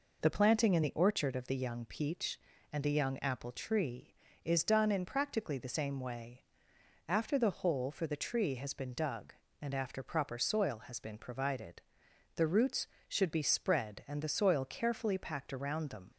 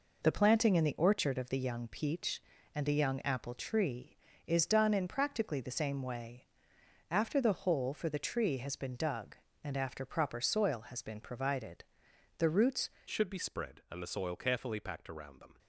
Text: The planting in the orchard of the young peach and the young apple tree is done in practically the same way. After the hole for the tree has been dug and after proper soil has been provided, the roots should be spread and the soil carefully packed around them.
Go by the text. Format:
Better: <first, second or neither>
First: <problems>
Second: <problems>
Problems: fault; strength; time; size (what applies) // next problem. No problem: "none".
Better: first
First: none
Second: changes voice at "should"; from 13.1 s on; 2.4 s long